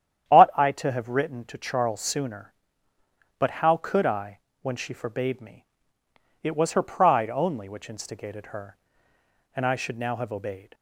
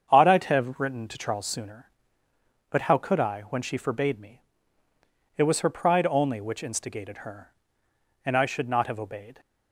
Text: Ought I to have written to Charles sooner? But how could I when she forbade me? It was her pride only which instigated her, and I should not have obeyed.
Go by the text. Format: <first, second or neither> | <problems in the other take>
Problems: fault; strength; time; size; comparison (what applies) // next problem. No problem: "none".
second | starts louder than the rest; strong; until 1.3 s; 9.5 dB; strong in the second // pauses between "I" and "when"; slight; at 4.3 s; 0.22 s long // says "now" for "not"; at 9.9 s